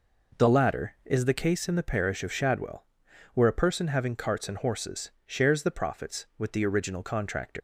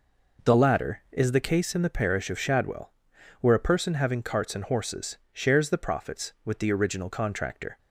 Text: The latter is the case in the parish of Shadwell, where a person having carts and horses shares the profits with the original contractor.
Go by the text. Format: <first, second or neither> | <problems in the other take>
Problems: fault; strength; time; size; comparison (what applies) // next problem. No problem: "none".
second | pauses between "horses" and "shares"; slight; at 5.1 s; 0.16 s long; slight in the second // leaves "contractor" unfinished; at 7.5 s; 110 ms